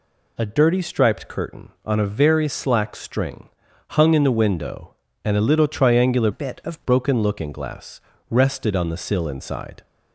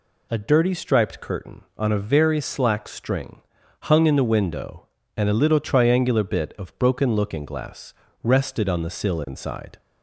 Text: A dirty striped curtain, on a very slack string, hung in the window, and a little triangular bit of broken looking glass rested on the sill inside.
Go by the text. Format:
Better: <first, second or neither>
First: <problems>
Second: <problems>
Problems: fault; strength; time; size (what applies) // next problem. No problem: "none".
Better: second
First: changes voice from "bit" to "of"; from 6.3 to 6.8 s; 0.5 s long // pauses between "glass" and "rested"; slight; at 8.0 s; 0.28 s long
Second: pauses between "glass" and "rested"; slight; at 7.9 s; 0.28 s long